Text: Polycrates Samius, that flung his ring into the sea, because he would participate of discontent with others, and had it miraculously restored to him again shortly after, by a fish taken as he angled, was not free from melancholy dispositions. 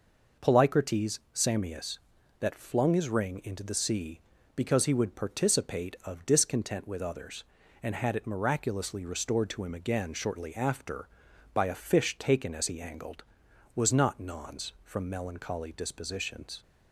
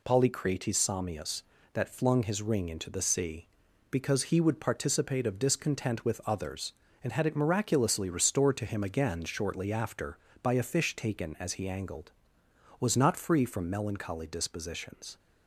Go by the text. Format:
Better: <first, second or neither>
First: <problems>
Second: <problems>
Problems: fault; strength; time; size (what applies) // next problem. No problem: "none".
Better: second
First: pauses between "Polycrates" and "Samius"; slight; at 1.1 s; 0.16 s long // says "nons" for "free"; at 14.1 s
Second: none